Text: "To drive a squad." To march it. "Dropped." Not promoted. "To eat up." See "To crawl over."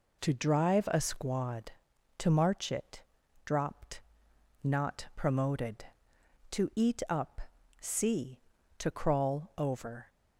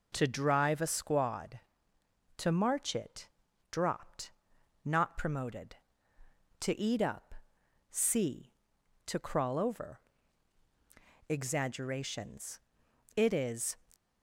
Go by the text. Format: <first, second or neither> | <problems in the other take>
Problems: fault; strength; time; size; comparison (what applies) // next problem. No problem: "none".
first | goes on to say "Exaggerations It is"; strong; from 11.2 s on; 2.4 s long